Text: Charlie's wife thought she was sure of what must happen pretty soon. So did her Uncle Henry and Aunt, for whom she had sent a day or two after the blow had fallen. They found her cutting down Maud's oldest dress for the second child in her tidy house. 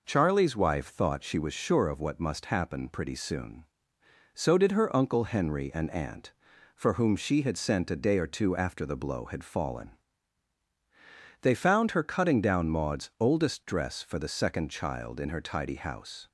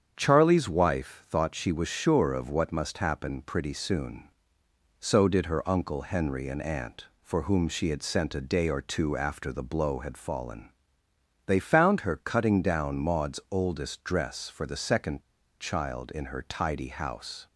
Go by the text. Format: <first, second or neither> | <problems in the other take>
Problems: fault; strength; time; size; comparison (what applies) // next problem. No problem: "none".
first | starts louder than the rest; strong; until 1.1 s; 8 dB // pauses between "second" and "child"; at 15.2 s; 0.39 s long